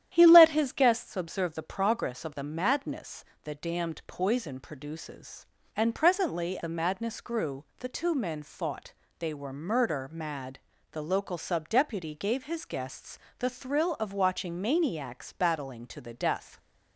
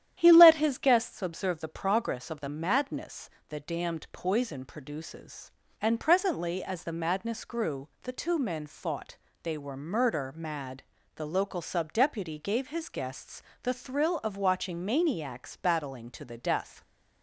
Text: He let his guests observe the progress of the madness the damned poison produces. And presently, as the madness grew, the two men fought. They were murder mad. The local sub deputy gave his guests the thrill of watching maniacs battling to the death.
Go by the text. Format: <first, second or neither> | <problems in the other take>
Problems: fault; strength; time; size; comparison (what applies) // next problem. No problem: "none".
second | starts louder than the rest; strong; until 1.1 s; 10.5 dB; strong in the second // pauses between "madness" and "the"; slight; at 3.2 s; 0.20 s long; slight in the second // skips "as"; at 6.5 s // pauses between "guests" and "the"; slight; at 13.1 s; 0.18 s long; slight in the second